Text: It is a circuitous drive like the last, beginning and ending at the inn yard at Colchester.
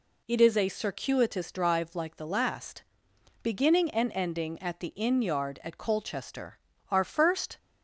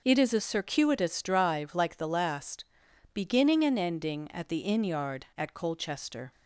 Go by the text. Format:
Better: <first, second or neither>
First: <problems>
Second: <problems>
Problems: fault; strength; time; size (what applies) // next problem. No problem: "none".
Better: second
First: goes on to say "Our first"; noticeable; from 6.8 s on; 0.68 s long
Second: none